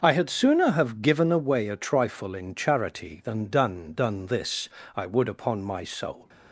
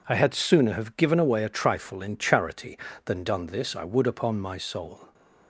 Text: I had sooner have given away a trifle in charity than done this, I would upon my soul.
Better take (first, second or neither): second